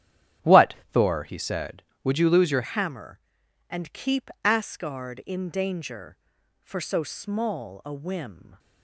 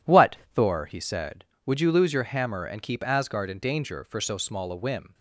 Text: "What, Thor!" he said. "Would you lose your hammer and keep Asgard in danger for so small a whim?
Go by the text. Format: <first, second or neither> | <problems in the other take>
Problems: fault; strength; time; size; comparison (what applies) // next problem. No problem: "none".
second | starts louder than the rest; strong; until 1.6 s; 11.5 dB // changes voice at "hammer"; from 2.6 s on; 5.9 s long